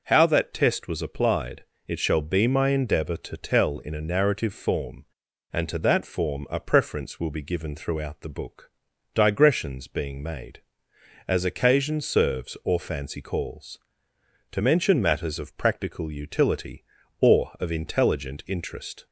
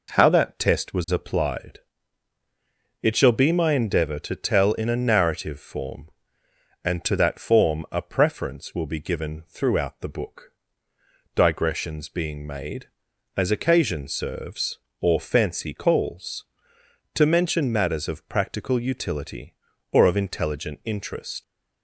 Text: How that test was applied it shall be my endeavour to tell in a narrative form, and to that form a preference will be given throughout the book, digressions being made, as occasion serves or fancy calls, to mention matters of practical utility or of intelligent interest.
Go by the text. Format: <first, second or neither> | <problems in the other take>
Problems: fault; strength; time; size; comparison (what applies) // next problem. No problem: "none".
first | pauses between "applied" and "it"; at 1.7 s; 1.2 s long; slight in the first // leaves "interest" unfinished; at 21.4 s; 90 ms